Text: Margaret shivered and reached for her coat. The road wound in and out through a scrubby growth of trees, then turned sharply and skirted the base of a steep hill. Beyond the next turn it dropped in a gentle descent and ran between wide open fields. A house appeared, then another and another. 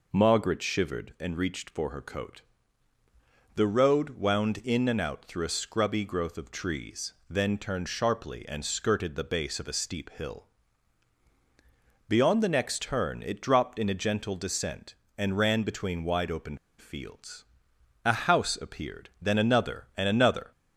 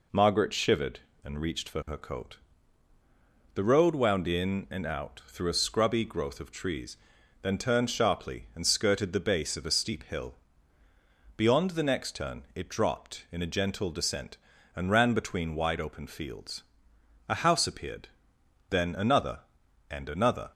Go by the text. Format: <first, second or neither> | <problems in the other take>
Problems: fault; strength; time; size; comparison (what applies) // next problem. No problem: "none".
second | pauses between "open" and "fields"; slight; at 16.5 s; 0.21 s long